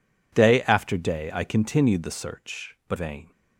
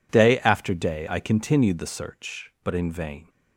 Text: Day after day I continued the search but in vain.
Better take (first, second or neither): second